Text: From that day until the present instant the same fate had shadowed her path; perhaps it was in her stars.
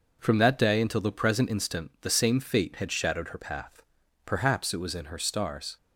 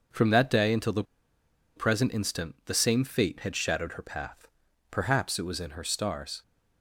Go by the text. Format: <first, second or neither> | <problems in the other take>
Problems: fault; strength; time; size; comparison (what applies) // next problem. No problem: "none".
first | pauses between "the" and "present"; noticeable; at 1.0 s; 0.72 s long